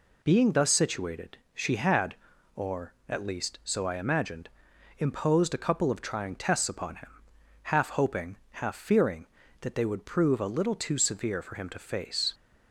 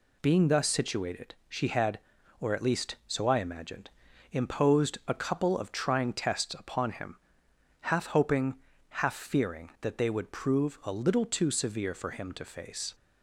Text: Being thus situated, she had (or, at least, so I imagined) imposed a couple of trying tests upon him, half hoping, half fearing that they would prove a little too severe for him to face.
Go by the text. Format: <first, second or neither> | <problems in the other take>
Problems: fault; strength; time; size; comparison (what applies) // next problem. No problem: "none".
neither | none